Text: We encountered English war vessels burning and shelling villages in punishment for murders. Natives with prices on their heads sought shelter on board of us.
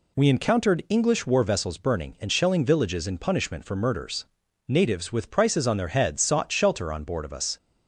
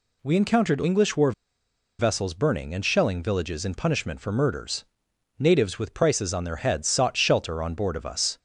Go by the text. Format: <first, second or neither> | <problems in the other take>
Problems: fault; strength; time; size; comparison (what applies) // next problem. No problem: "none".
first | pauses between "war" and "vessels"; noticeable; at 1.3 s; 0.67 s long